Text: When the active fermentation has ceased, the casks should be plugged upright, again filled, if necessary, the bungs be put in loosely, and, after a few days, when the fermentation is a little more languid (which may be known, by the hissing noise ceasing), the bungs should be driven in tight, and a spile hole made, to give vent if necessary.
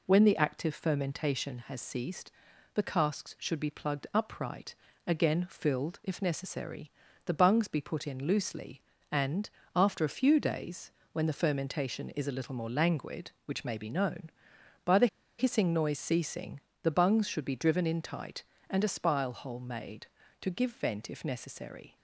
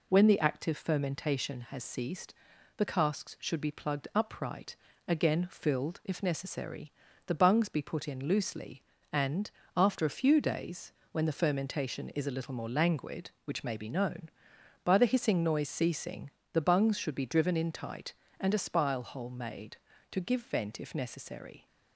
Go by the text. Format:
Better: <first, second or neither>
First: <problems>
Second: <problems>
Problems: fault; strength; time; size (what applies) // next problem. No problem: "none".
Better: second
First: pauses between "the" and "hissing"; slight; at 15.0 s; 0.32 s long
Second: none